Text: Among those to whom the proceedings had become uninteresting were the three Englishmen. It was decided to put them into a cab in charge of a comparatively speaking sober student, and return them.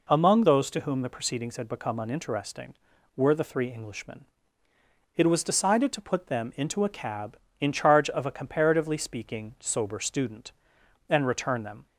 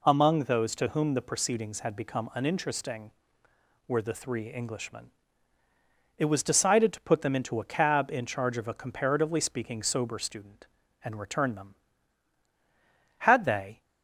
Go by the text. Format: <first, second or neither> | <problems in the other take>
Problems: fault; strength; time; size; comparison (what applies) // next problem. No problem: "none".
first | goes on to say "Had they"; noticeable; from 13.1 s on; 0.62 s long